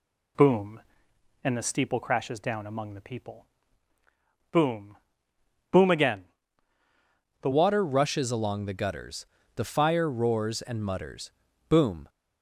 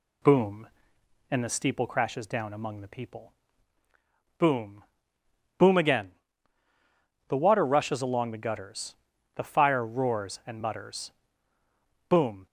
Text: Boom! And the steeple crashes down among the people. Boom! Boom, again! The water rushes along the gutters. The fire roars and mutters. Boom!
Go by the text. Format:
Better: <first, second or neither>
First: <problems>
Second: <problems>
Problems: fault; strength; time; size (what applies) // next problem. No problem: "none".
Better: second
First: changes voice at "water"; from 7.5 s on; 4.5 s long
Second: none